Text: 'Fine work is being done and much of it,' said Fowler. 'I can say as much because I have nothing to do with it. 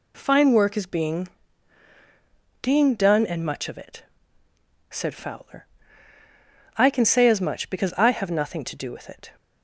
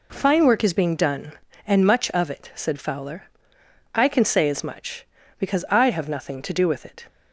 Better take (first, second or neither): second